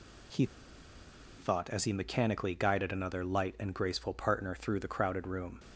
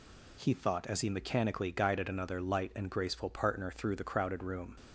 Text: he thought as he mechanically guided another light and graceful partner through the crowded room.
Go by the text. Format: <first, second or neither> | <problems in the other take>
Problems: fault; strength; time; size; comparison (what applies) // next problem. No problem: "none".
second | pauses between "he" and "thought"; noticeable; at 0.4 s; 0.92 s long